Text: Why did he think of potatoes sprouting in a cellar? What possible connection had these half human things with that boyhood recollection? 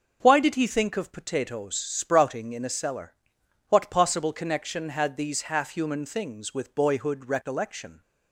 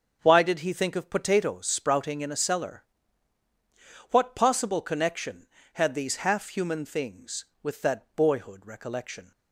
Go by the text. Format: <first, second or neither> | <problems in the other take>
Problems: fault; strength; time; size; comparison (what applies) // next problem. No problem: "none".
second | starts louder than the rest; until 1.2 s; 6.5 dB; also in the second // skips "that"; at 6.7 s